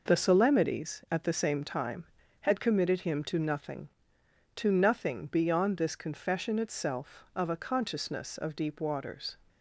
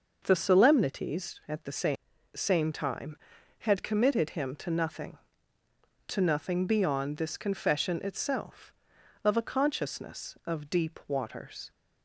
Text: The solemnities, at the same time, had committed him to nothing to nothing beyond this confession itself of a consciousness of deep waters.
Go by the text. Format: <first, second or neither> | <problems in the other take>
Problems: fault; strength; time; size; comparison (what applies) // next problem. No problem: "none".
first | starts louder than the rest; noticeable; until 1.2 s; 6 dB // says "same" twice; at 2.3 s